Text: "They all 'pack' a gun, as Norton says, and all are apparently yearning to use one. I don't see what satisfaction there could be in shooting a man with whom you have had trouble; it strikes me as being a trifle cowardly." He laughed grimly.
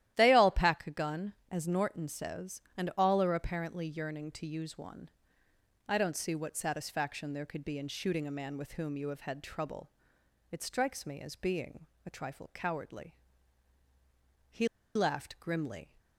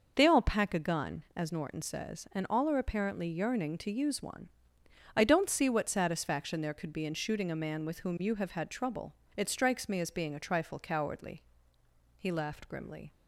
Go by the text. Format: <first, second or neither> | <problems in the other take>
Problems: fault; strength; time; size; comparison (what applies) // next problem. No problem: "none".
second | starts louder than the rest; strong; until 1.1 s; 13 dB // pauses between "being" and "a"; slight; at 11.8 s; 0.18 s long // pauses between "He" and "laughed"; slight; at 14.6 s; 0.28 s long